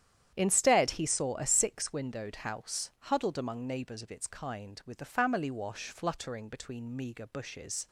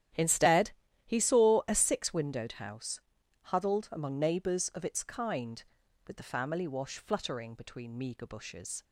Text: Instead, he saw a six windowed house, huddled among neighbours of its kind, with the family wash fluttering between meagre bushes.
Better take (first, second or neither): neither